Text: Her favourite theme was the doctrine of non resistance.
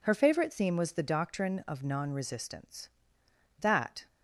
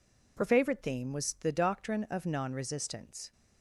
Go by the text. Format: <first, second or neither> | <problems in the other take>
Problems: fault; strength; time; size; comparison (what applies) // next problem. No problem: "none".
second | goes on to say "That"; slight; from 3.5 s on; 0.48 s long